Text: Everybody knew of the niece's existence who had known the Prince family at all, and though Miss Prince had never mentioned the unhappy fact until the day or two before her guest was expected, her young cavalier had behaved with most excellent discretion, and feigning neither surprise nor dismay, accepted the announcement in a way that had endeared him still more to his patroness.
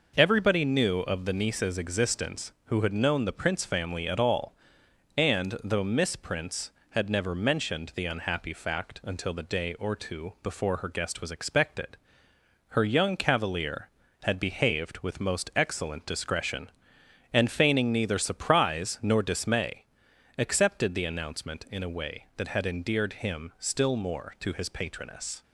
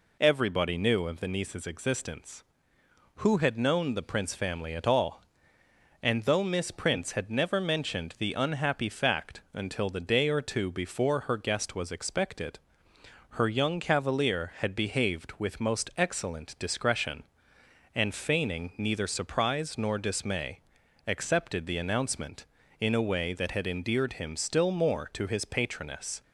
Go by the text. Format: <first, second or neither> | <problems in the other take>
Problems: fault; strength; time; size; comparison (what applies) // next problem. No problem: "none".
neither | none